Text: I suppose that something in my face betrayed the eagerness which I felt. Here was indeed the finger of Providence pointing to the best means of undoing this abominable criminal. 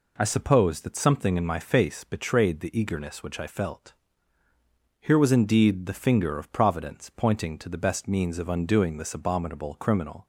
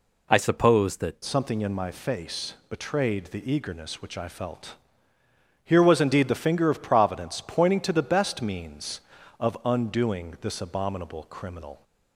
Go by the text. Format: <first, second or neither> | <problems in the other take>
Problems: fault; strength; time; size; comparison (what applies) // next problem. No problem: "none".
first | changes voice at "something"; from 1.2 s on; 10.6 s long // pauses between "face" and "betrayed"; slight; at 2.5 s; 0.16 s long